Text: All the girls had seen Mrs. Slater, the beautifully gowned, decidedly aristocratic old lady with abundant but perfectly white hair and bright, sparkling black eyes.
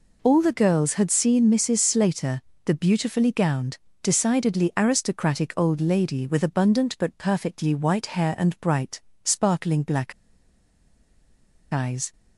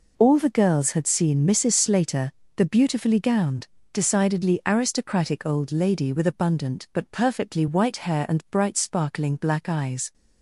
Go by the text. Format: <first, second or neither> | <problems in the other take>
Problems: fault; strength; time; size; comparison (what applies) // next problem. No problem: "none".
second | pauses between "black" and "eyes"; strong; at 10.1 s; 1.5 s long